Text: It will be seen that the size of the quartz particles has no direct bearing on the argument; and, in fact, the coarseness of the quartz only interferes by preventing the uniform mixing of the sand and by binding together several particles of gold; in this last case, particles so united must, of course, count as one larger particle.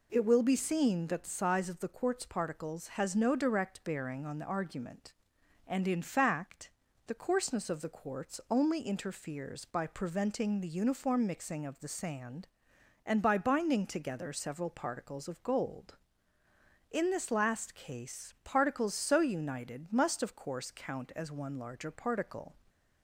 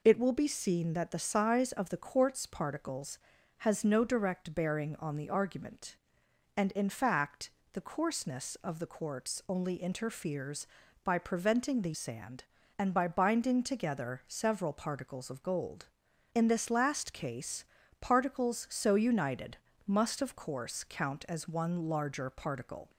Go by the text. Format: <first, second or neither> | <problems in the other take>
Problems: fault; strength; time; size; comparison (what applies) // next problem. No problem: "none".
first | skips "uniform mixing of the"; at 11.9 s // pauses between "united" and "must"; slight; at 19.5 s; 0.28 s long